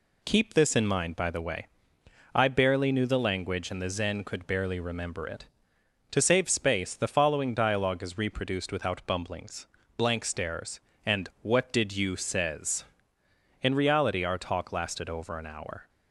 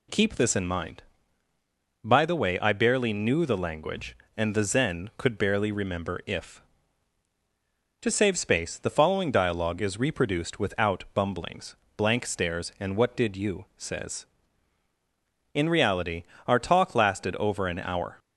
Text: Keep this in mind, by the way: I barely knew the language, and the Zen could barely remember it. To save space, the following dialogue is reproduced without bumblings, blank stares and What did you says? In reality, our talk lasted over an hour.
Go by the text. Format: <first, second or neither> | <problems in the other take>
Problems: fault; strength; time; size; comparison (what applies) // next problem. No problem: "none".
first | says "if" for "it"; at 6.2 s